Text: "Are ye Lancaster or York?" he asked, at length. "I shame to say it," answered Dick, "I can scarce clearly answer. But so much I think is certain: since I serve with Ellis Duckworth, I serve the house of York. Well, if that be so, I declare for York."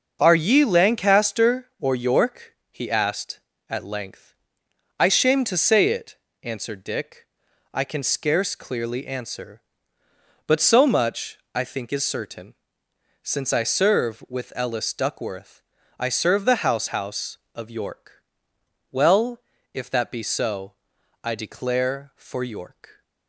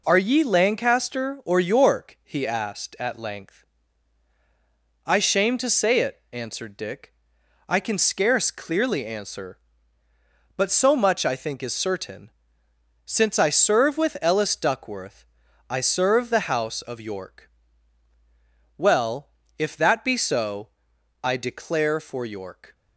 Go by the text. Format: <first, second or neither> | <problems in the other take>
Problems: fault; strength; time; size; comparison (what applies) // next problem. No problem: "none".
second | starts louder than the rest; until 1.2 s; 6.5 dB // pauses between "much" and "I"; slight; at 11.3 s; 0.16 s long // says "house" twice; at 16.8 s